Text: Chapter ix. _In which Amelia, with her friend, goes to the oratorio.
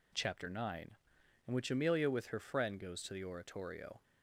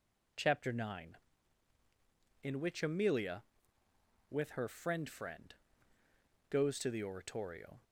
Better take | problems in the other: first | says "friend" twice; at 5.0 s

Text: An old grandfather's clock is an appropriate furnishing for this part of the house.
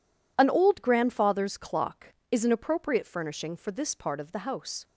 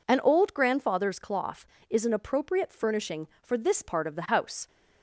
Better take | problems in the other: first | says "cloth" for "clock"; at 1.1 s

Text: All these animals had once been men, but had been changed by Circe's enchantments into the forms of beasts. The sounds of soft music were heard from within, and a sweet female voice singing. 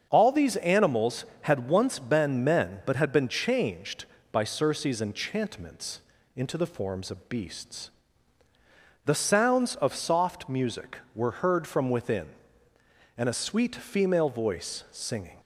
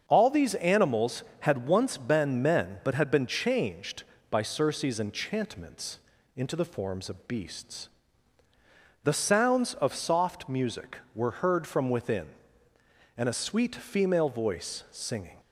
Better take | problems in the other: neither | starts louder than the rest; the same in both // pauses between "enchantments" and "into"; the same in both

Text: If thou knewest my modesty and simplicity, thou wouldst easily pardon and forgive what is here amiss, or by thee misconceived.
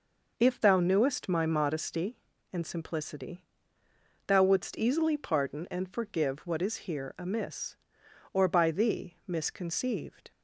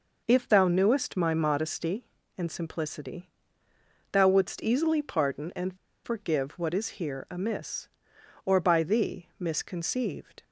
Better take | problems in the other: first | pauses between "and" and "forgive"; slight; at 5.7 s; 0.27 s long

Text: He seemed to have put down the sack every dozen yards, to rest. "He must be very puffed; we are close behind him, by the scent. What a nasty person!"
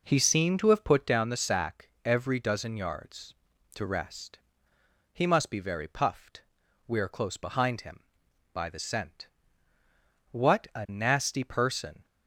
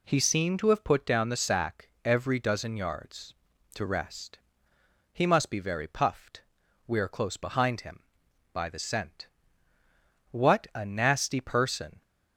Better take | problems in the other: second | starts louder than the rest; noticeable; until 1.2 s; 4.5 dB // pauses between "sack" and "every"; slight; at 1.8 s; 0.16 s long; slight in the second

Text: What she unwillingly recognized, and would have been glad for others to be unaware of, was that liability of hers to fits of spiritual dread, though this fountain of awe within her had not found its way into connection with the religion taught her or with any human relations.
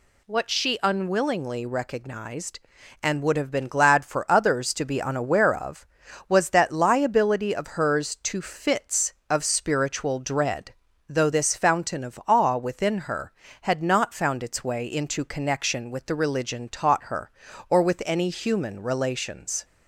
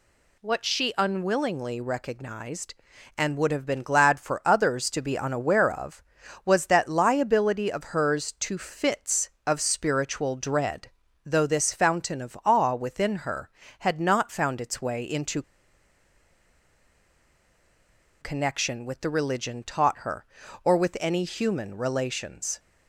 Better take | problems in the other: first | pauses between "into" and "connection"; strong; at 15.4 s; 2.7 s long

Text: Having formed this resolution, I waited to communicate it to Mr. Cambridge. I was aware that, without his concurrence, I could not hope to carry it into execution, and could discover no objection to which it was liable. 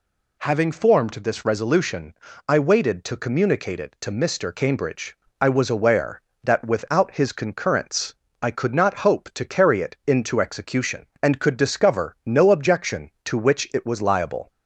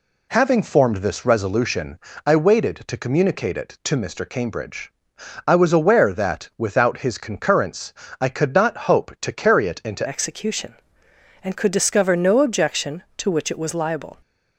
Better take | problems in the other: first | changes voice at "execution"; from 10.0 s on; 4.1 s long

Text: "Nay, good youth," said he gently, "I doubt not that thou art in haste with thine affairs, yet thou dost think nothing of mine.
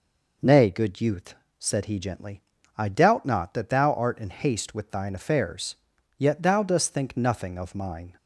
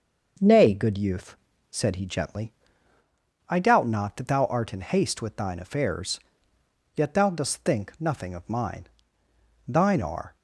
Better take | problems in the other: first | goes on to say "Thine are"; noticeable; from 9.6 s on; 0.68 s long

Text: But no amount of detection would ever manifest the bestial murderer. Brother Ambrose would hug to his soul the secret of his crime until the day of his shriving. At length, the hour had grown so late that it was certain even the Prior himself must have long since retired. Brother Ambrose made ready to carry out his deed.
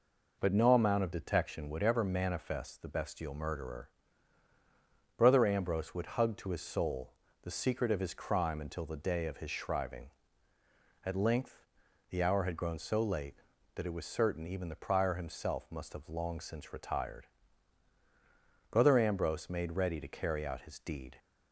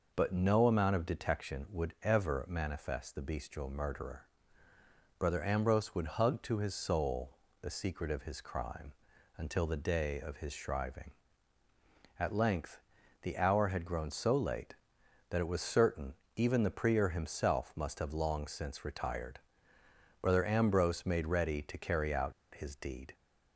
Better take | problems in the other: first | pauses between "soul" and "the"; slight; at 7.3 s; 0.24 s long; slight in the first // pauses between "crime" and "until"; noticeable; at 8.9 s; 0.46 s long // pauses between "certain" and "even"; slight; at 16.1 s; 0.22 s long // pauses between "out" and "his"; slight; at 22.3 s; 0.21 s long

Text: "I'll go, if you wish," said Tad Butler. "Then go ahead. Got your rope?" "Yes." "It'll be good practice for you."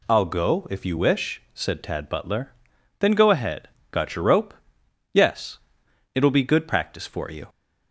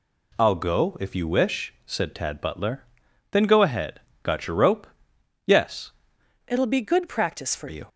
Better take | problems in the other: first | changes voice from "It'll" to "for"; from 6.4 to 7.6 s; 1.2 s long

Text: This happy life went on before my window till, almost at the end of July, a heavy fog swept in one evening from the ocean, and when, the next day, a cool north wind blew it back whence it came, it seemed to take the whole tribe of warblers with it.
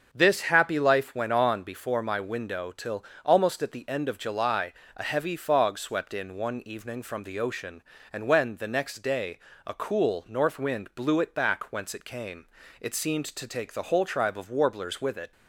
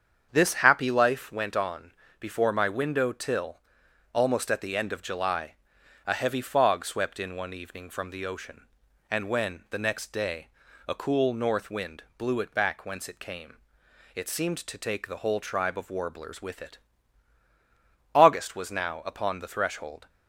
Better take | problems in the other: first | starts louder than the rest; strong; until 1.3 s; 7.5 dB; also in the first // pauses between "on" and "before"; slight; at 1.9 s; 0.28 s long // pauses between "wind" and "blew"; slight; at 12.0 s; 0.16 s long // goes on to say "August was now upon the threshold"; strong; from 18.1 s on; 1.9 s long

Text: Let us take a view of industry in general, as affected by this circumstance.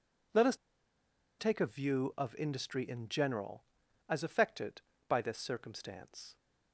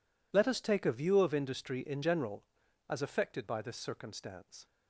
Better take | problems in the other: second | pauses between "us" and "take"; noticeable; at 0.5 s; 0.83 s long

